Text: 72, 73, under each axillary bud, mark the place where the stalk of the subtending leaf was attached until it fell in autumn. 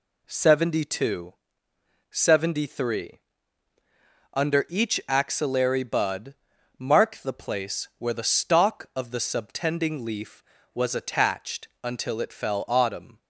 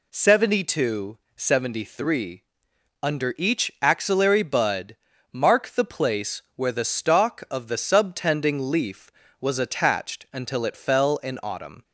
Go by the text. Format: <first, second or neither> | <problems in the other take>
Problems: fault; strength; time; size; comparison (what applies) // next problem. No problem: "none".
second | pauses between "attached" and "until"; slight; at 11.6 s; 0.16 s long // skips "in"; at 12.6 s